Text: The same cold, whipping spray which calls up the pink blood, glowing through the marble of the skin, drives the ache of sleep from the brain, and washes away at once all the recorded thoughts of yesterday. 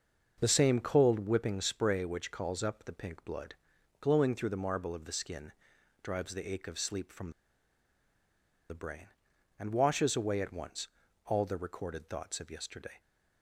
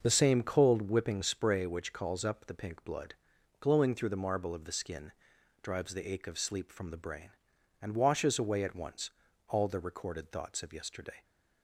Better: second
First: starts louder than the rest; noticeable; until 1.4 s; 6 dB // pauses between "from" and "the"; strong; at 7.3 s; 1.3 s long // pauses between "once" and "all"; at 10.8 s; 0.38 s long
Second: starts louder than the rest; noticeable; until 1.0 s; 6 dB // pauses between "once" and "all"; at 9.1 s; 0.38 s long

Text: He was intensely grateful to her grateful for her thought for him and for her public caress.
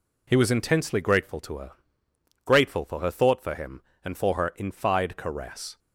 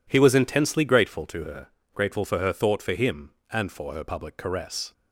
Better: second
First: pauses between "her" and "grateful"; noticeable; at 1.7 s; 0.74 s long // says "infide" for "public"; at 4.5 s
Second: pauses between "her" and "grateful"; slight; at 1.6 s; 0.28 s long

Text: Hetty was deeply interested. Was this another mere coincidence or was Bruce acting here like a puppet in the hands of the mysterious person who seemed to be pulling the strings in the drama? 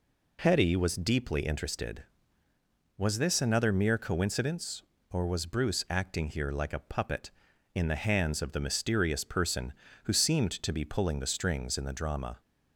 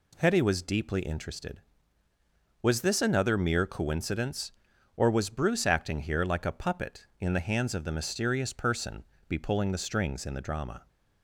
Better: first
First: none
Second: skips "who seemed to"; at 9.1 s

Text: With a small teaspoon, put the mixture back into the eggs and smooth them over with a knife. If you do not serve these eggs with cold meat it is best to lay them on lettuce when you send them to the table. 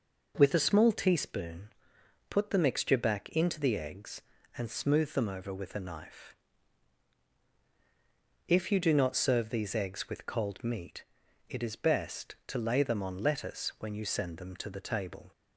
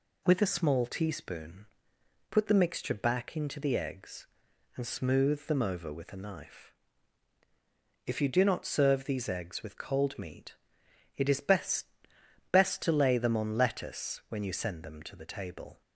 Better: first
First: pauses between "meat" and "it"; at 11.0 s; 0.44 s long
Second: pauses between "meat" and "it"; noticeable; at 10.5 s; 0.64 s long // says "best" twice; at 12.5 s

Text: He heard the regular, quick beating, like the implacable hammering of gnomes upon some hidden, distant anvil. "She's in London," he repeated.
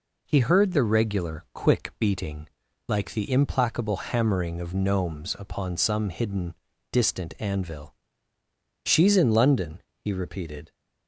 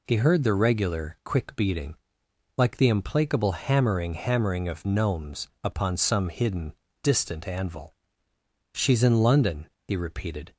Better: first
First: none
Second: says "hammering" twice; at 4.1 s // pauses between "gnomes" and "upon"; slight; at 5.4 s; 0.16 s long

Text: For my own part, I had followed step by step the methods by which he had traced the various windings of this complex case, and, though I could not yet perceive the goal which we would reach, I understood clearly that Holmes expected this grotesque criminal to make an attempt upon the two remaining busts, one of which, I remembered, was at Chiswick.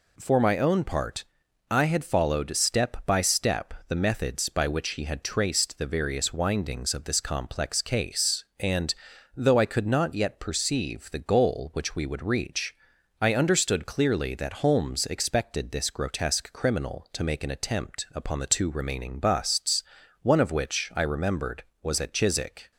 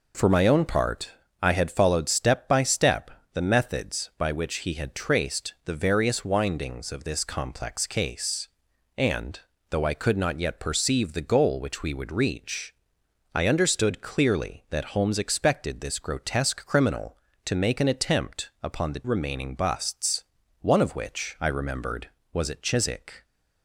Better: first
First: pauses between "step" and "the"; slight; at 3.7 s; 0.16 s long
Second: pauses between "step" and "the"; slight; at 3.0 s; 0.24 s long // skips "two"; at 19.0 s

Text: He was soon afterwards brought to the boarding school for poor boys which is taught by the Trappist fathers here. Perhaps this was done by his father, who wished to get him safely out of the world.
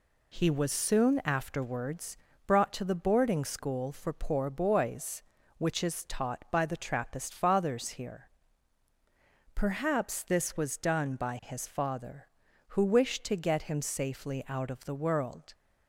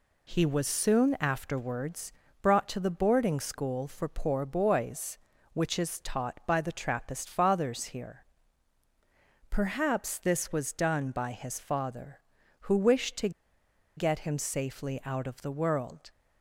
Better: first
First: pauses between "afterwards" and "brought"; slight; at 2.1 s; 0.30 s long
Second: pauses between "afterwards" and "brought"; slight; at 2.1 s; 0.30 s long // pauses between "to" and "get"; noticeable; at 13.2 s; 0.66 s long

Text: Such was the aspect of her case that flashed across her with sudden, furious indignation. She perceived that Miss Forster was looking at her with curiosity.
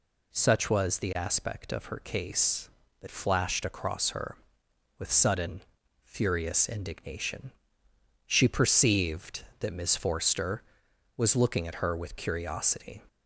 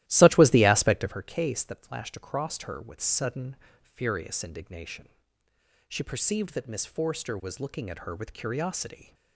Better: first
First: none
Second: starts louder than the rest; strong; until 1.2 s; 15 dB

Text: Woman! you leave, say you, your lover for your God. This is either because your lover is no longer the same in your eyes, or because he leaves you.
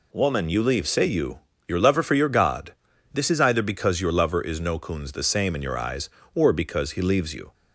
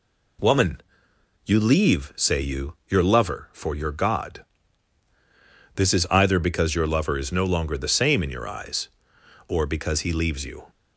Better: second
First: says "coons" for "longer"; at 4.7 s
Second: none

